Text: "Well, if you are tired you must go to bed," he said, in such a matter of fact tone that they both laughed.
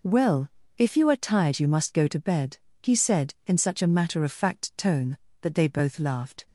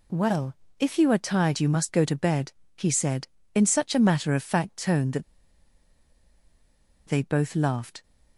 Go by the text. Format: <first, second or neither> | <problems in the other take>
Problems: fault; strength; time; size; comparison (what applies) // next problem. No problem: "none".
first | pauses between "that" and "they"; strong; at 5.2 s; 1.8 s long